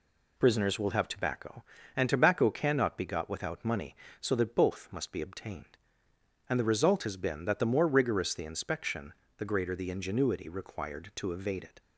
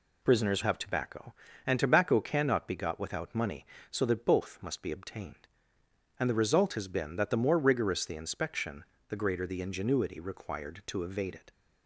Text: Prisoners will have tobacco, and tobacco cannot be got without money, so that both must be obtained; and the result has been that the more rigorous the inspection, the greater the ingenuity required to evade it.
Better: first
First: none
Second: skips "will"; at 0.6 s

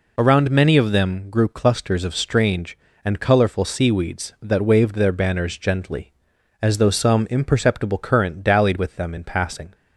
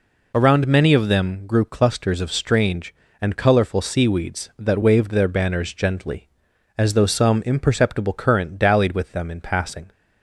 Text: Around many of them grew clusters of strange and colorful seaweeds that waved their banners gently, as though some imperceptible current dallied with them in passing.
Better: neither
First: none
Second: none

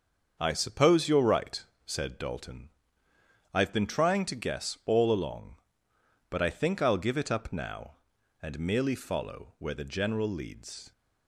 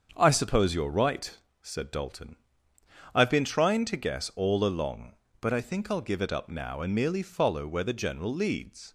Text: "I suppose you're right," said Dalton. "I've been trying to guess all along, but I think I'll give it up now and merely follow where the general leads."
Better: neither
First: starts louder than the rest; until 1.4 s; 6.5 dB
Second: starts louder than the rest; until 1.1 s; 7 dB

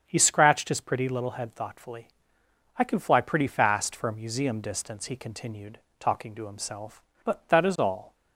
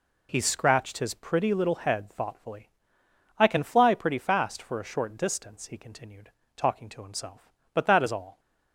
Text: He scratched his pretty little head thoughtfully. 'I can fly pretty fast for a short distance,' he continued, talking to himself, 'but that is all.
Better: second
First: starts louder than the rest; strong; until 1.0 s; 7.5 dB // says "museum" for "short"; at 4.1 s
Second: none

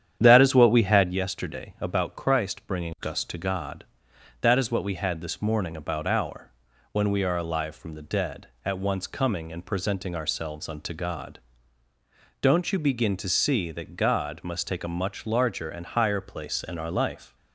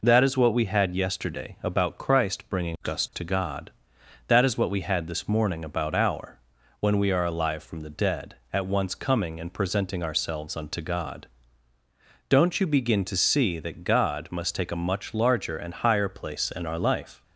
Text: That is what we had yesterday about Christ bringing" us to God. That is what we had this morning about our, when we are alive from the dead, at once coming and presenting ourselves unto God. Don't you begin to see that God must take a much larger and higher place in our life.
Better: second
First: starts louder than the rest; strong; until 1.2 s; 9.5 dB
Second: none

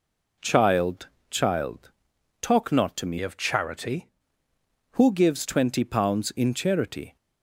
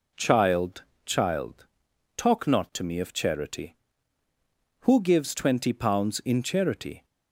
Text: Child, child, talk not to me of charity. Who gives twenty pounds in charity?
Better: second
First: changes voice from "of" to "charity"; from 3.2 to 4.0 s; 0.8 s long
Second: none

